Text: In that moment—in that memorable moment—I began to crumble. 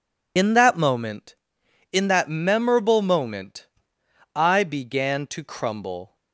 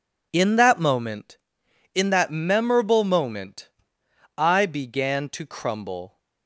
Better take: second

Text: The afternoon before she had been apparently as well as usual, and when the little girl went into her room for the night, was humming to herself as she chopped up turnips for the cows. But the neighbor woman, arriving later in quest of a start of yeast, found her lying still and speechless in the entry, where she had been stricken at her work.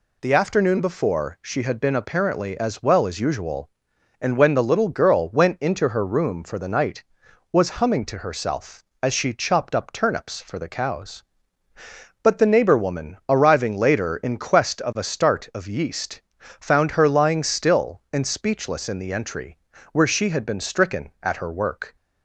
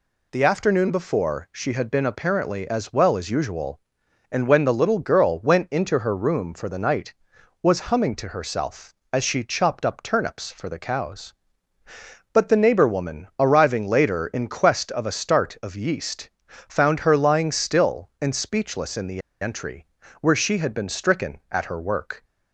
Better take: first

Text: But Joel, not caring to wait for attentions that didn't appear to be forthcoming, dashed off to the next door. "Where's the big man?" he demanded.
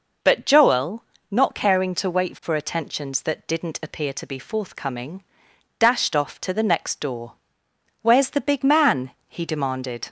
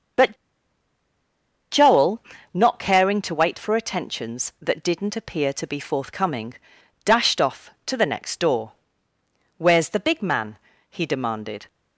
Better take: first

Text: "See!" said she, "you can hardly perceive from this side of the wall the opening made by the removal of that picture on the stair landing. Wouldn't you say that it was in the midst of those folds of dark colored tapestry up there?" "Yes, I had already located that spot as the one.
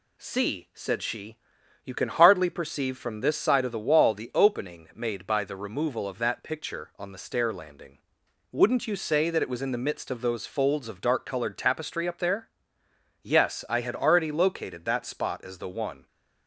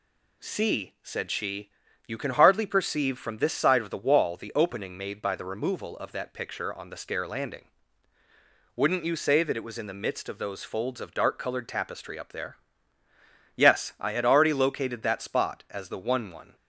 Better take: first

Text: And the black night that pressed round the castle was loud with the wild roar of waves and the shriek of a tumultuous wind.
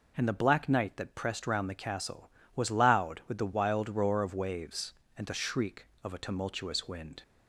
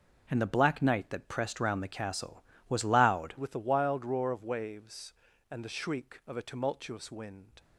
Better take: first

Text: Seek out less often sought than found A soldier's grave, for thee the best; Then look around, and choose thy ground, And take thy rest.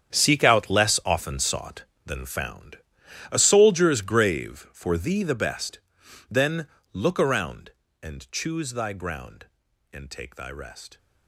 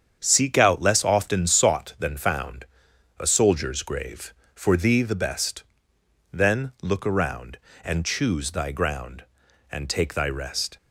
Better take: second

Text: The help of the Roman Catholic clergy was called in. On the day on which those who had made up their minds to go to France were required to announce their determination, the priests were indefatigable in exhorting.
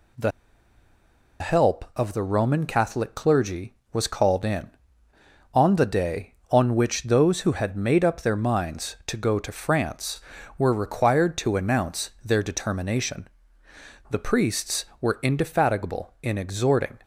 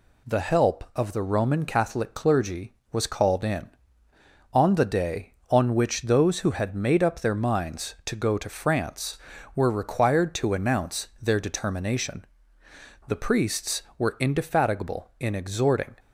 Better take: second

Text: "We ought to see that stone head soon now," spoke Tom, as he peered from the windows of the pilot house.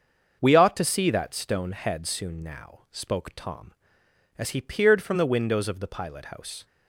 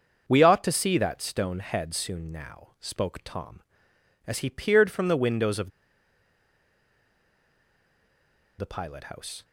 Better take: first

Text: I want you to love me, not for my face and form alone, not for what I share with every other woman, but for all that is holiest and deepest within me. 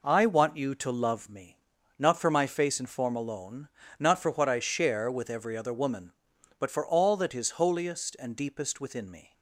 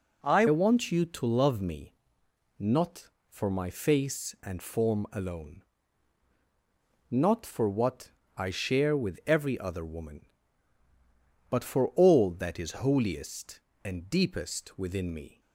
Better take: first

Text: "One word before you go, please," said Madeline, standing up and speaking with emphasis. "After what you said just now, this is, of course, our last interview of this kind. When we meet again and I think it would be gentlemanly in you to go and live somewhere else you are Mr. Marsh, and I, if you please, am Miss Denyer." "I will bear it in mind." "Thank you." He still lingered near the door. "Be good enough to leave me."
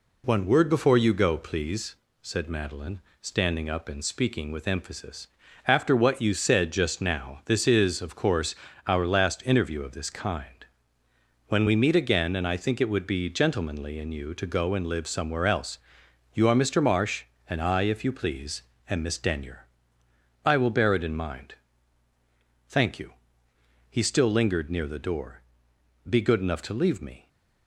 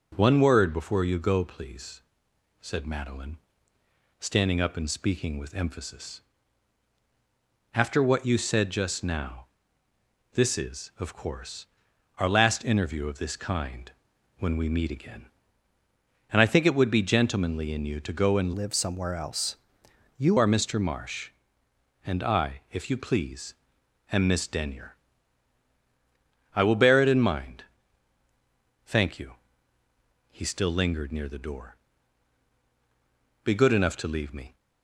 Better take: first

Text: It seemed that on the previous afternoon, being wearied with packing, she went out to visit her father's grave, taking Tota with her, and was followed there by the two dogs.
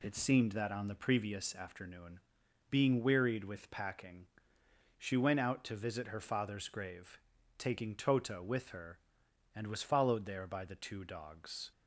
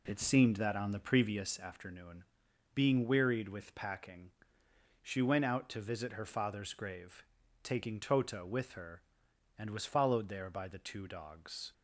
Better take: first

